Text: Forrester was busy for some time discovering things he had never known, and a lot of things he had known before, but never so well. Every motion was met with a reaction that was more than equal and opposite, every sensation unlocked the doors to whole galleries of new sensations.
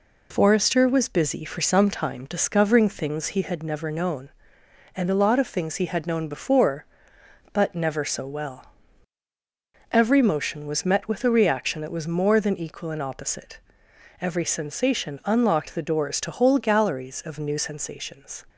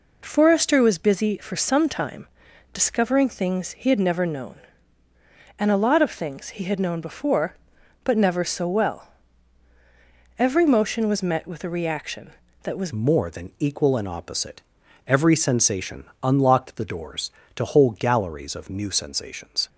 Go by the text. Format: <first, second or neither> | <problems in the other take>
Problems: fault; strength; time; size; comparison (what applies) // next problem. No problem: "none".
first | pauses between "time" and "discovering"; noticeable; at 2.2 s; 0.46 s long // changes voice at "more"; from 12.9 s on; 6.7 s long // pauses between "sensation" and "unlocked"; slight; at 16.0 s; 0.18 s long